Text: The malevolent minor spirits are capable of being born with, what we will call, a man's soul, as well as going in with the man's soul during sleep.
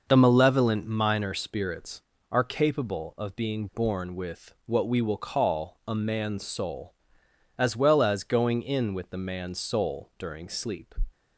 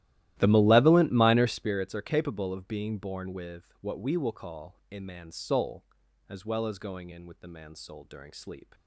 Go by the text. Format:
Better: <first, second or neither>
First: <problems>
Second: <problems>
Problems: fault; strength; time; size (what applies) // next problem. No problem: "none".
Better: first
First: none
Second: starts louder than the rest; strong; until 1.7 s; 14.5 dB